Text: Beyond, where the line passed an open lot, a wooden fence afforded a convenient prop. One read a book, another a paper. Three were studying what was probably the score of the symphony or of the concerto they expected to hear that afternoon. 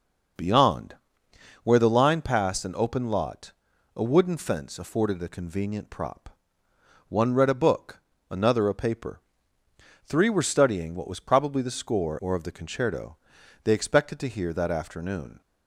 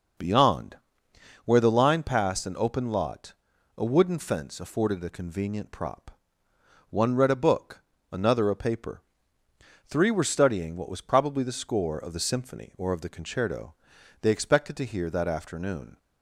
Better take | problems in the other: second | skips "of the symphony"; at 12.1 s // pauses between "concerto" and "they"; noticeable; at 13.1 s; 0.48 s long; noticeable in the second

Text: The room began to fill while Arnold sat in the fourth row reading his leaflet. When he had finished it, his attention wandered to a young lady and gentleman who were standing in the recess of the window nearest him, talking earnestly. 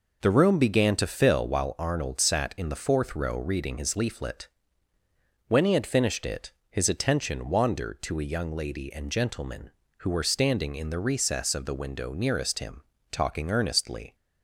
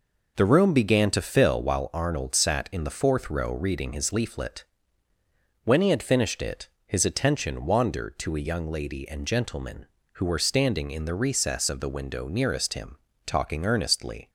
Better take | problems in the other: neither | none

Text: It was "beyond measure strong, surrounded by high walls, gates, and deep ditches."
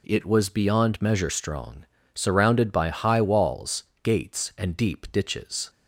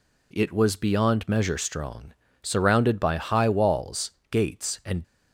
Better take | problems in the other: first | stops before "deep ditches"; at 5.0 s

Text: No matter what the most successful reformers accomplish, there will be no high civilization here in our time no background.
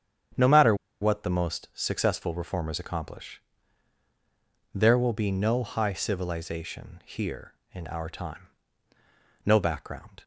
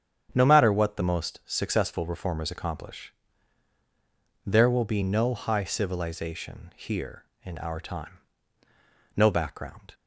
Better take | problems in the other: second | starts louder than the rest; strong; until 1.6 s; 8.5 dB; strong in the second // pauses between "matter" and "what"; slight; at 0.7 s; 0.26 s long // pauses between "time" and "no"; at 8.4 s; 1.0 s long; also in the second

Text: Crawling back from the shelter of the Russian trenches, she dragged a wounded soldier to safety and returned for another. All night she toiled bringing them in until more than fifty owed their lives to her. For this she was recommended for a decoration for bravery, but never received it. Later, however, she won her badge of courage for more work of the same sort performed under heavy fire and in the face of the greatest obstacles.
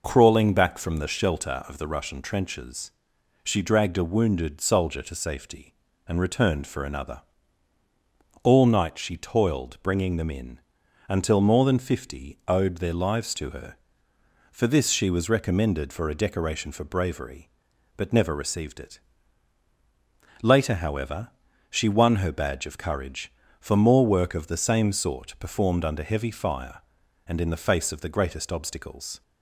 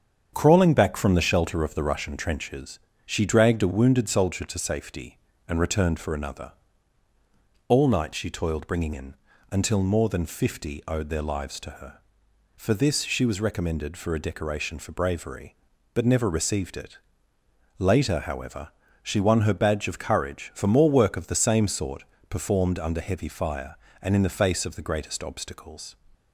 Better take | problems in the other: first | starts louder than the rest; strong; until 1.3 s; 7.5 dB // skips "them"; at 8.9 s // pauses between "in" and "until"; at 9.1 s; 0.38 s long; noticeable in the first // pauses between "sort" and "performed"; slight; at 22.0 s; 0.26 s long

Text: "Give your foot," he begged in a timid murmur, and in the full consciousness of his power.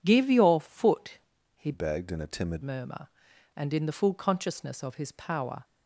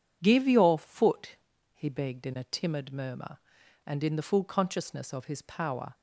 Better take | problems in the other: second | changes voice from "begged" to "timid"; from 1.7 to 2.6 s; 0.9 s long

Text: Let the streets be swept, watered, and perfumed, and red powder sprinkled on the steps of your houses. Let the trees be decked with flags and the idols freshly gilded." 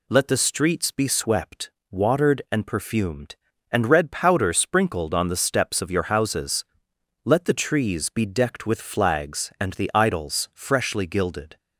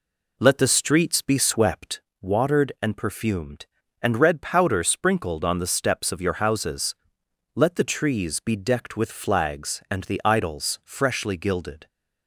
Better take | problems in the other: first | starts louder than the rest; slight; until 2.1 s; 3 dB

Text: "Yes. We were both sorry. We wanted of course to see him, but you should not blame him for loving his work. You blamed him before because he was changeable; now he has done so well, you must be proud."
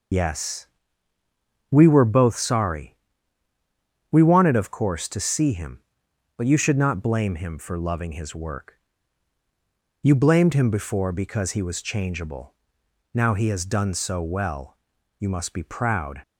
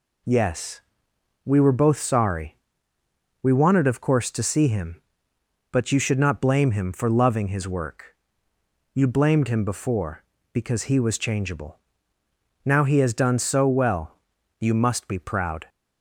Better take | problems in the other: second | loses the start of "Yes"; at 0.1 s; 90 ms

